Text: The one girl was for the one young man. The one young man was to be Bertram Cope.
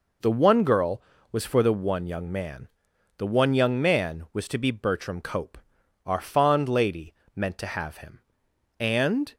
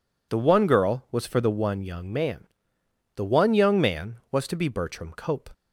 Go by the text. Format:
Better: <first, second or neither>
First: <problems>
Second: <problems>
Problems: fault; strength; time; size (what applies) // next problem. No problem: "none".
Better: second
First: goes on to say "Our fond lady meant to have him and"; strong; from 6.0 s on; 3.3 s long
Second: none